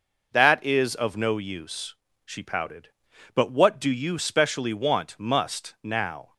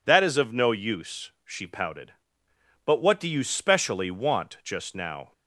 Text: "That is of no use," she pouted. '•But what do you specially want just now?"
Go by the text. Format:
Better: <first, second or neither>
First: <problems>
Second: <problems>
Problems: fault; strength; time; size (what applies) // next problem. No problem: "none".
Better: second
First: says "must" for "just"; at 5.1 s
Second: none